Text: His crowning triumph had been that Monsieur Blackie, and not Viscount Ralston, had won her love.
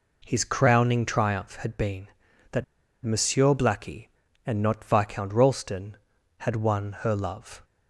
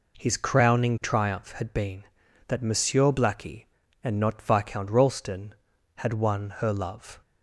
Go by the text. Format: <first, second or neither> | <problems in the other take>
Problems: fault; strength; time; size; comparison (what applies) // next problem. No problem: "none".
second | pauses between "that" and "Monsieur"; at 2.6 s; 0.39 s long